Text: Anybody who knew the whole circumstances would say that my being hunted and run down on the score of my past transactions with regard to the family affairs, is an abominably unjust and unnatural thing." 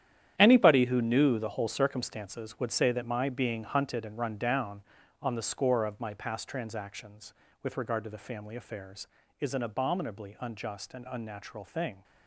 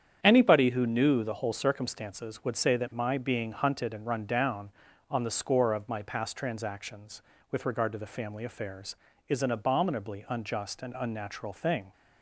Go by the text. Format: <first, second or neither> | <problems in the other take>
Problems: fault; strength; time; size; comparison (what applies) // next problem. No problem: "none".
second | gets quieter; strong; throughout; 12.5 dB // starts louder than the rest; strong; until 1.3 s; 10 dB; strong in the second